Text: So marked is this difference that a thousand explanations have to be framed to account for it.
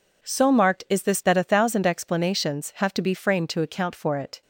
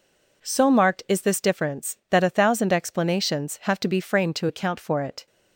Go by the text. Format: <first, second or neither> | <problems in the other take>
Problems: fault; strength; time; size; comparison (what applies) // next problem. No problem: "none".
second | skips "difference"; at 1.2 s